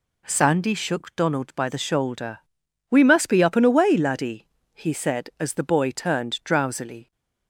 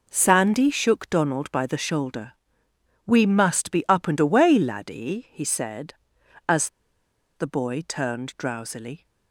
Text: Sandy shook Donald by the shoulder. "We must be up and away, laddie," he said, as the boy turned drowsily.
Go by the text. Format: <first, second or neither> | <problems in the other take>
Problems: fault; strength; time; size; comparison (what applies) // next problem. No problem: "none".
first | pauses between "as" and "the"; noticeable; at 6.6 s; 0.67 s long